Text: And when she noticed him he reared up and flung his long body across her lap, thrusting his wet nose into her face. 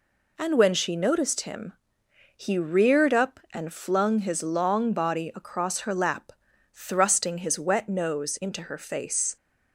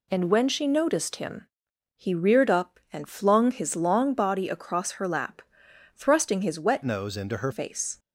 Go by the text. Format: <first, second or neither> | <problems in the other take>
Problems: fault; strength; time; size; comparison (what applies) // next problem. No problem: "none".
first | pauses between "him" and "he"; noticeable; at 1.4 s; 0.54 s long; noticeable in the first // changes voice from "nose" to "her"; from 6.8 to 7.5 s; 0.7 s long